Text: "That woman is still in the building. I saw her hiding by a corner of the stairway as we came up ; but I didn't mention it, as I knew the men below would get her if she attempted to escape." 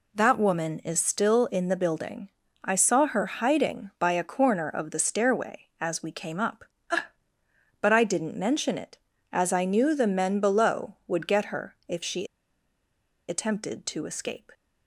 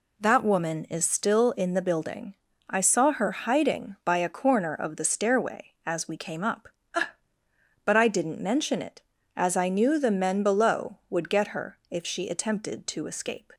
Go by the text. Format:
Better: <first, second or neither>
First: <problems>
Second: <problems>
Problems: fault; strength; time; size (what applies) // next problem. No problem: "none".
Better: second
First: pauses between "she" and "attempted"; at 12.2 s; 1.0 s long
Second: none